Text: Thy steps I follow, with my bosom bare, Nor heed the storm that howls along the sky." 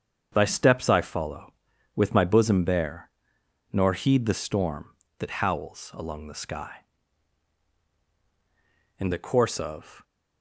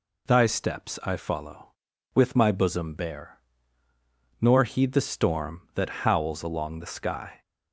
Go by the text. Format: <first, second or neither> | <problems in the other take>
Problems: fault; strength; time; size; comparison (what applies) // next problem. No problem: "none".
second | starts louder than the rest; strong; until 1.3 s; 7 dB // goes on to say "In the course of"; noticeable; from 8.9 s on; 1.0 s long